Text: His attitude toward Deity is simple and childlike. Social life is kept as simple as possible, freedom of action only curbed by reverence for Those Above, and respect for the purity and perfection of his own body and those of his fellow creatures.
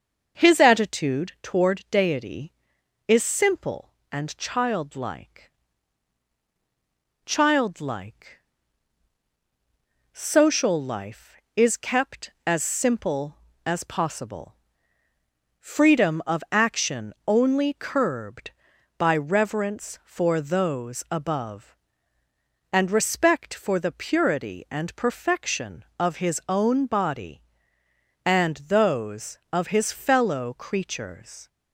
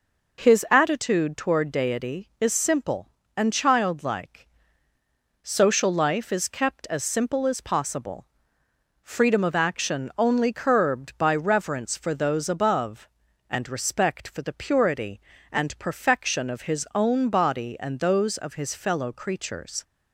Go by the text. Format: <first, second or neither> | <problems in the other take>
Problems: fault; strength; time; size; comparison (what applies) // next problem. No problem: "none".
second | starts louder than the rest; noticeable; until 1.4 s; 6 dB // says "childlike" twice; at 7.2 s